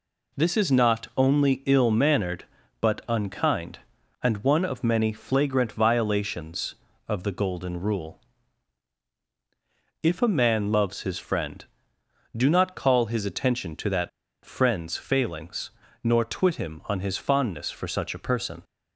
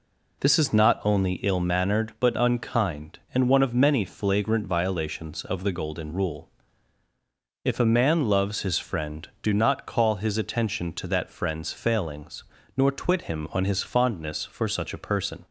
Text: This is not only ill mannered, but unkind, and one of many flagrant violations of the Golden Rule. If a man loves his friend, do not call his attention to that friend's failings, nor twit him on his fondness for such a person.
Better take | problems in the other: second | pauses between "that" and "friend's"; slight; at 14.0 s; 0.35 s long

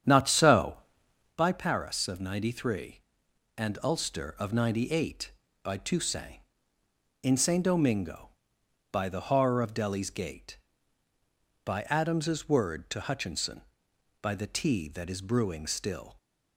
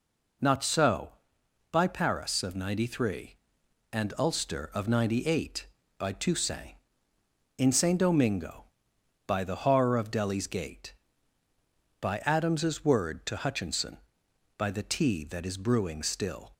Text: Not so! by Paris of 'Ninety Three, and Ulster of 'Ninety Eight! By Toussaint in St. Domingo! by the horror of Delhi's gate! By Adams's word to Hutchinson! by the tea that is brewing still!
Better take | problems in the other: second | starts louder than the rest; strong; until 1.4 s; 8.5 dB

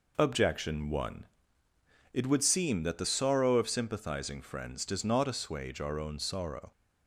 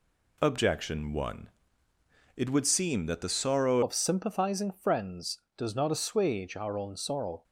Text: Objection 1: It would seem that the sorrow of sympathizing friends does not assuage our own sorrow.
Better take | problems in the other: first | changes voice at "of"; from 3.8 s on; 3.6 s long

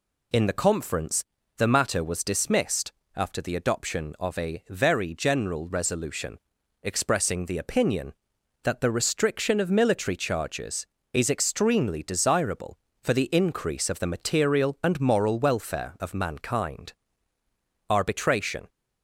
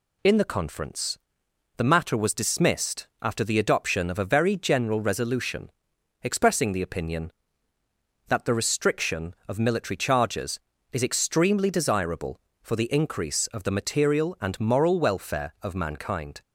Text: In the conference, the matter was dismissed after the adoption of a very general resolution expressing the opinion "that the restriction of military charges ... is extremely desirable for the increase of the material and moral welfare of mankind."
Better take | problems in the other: second | pauses between "dismissed" and "after"; slight; at 2.9 s; 0.24 s long; slight in the second // pauses between "resolution" and "expressing"; noticeable; at 6.3 s; 0.46 s long; noticeable in the second // goes on to say "ARBITRATION"; noticeable; from 17.8 s on; 0.80 s long

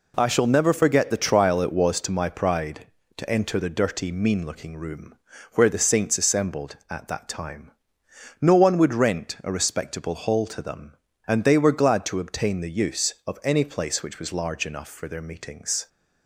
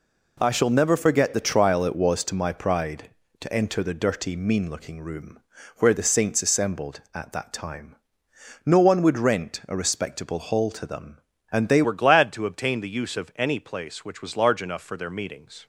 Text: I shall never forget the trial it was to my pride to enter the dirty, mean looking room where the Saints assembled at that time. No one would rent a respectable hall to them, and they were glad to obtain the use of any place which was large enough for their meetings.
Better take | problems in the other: first | pauses between "room" and "where"; at 5.4 s; 0.38 s long; also in the first // changes voice at "were"; from 11.8 s on; 3.8 s long

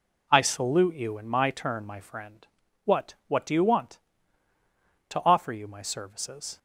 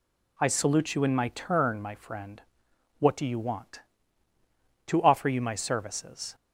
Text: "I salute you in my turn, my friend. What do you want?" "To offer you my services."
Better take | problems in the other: second | says "What" twice; at 3.2 s

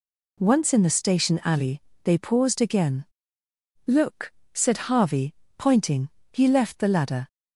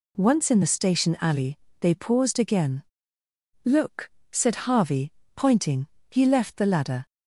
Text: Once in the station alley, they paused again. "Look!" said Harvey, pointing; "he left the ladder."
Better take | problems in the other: neither | none

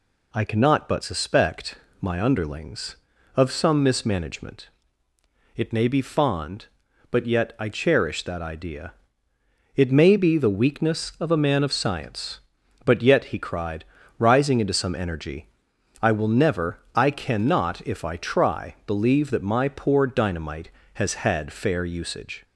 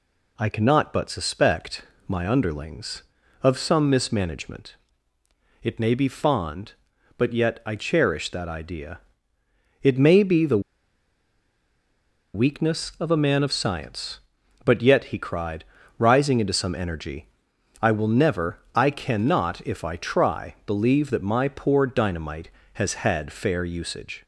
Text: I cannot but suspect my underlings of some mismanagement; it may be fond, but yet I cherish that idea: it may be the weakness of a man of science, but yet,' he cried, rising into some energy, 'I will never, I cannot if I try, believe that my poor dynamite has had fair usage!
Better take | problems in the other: first | pauses between "suspect" and "my"; slight; at 1.8 s; 0.26 s long; slight in the first // pauses between "the" and "weakness"; strong; at 10.5 s; 1.7 s long

